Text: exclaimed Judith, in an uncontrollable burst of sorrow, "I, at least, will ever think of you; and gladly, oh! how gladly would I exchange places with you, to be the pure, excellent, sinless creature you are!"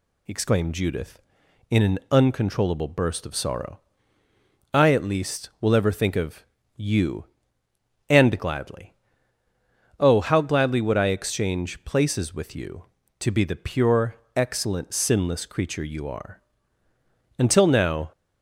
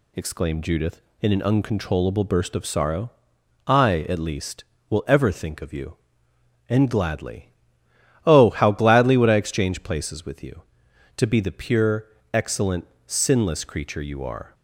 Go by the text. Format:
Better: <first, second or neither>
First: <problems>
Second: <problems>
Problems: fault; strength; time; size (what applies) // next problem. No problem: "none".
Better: second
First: pauses between "of" and "you"; slight; at 6.4 s; 0.32 s long // goes on to say "Until now"; noticeable; from 17.3 s on; 0.74 s long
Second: none